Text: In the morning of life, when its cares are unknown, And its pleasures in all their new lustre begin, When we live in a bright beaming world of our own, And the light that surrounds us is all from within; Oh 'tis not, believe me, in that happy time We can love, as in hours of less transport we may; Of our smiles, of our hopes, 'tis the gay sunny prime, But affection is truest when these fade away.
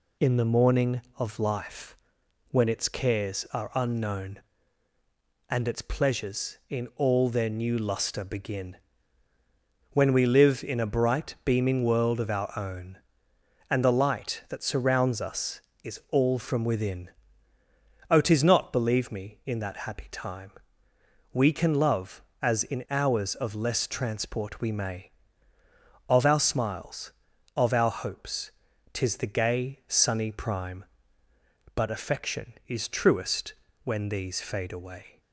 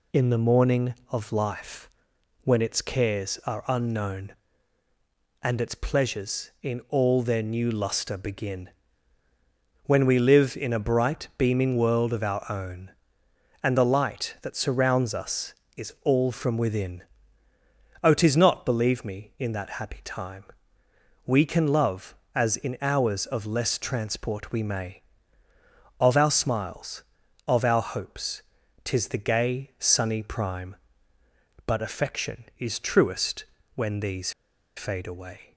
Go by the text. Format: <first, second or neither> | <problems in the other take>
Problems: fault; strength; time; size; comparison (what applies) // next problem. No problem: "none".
first | pauses between "time" and "We"; noticeable; at 20.4 s; 0.82 s long; noticeable in the first // pauses between "truest" and "when"; slight; at 33.4 s; 0.30 s long; slight in the first // pauses between "these" and "fade"; at 34.3 s; 0.45 s long